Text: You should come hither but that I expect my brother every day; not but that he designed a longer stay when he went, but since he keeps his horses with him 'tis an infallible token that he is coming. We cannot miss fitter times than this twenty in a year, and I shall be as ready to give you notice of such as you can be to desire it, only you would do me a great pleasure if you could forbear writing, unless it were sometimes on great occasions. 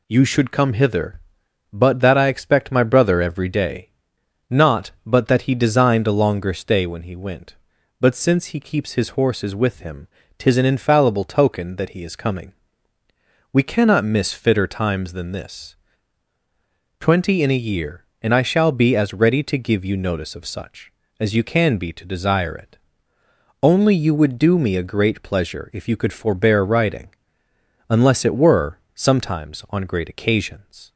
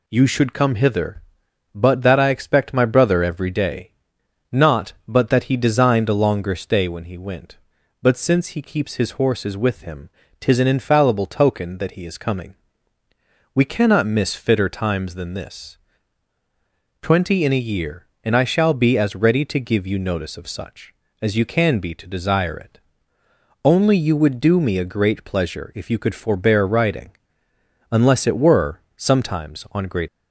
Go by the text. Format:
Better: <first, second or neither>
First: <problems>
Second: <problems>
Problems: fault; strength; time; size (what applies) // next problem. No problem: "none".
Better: first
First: pauses between "him" and "tis"; slight; at 10.0 s; 0.32 s long // pauses between "this" and "twenty"; strong; at 15.7 s; 1.2 s long // pauses between "were" and "sometimes"; slight; at 28.7 s; 0.18 s long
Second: pauses between "him" and "tis"; slight; at 10.0 s; 0.32 s long // pauses between "this" and "twenty"; strong; at 15.7 s; 1.2 s long // pauses between "were" and "sometimes"; slight; at 28.8 s; 0.18 s long // stops before "occasions"; at 30.0 s